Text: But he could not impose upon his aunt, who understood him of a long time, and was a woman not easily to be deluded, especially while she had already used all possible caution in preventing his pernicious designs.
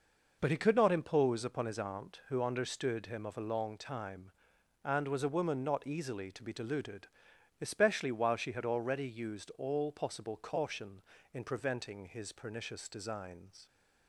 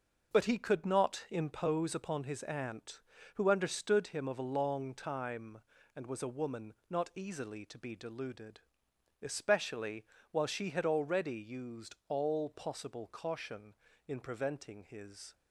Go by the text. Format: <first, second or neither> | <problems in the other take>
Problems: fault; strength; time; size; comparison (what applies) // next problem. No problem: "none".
first | pauses between "woman" and "not"; slight; at 6.7 s; 0.16 s long // pauses between "especially" and "while"; slight; at 10.0 s; 0.24 s long // stops before "pernicious designs"; at 15.3 s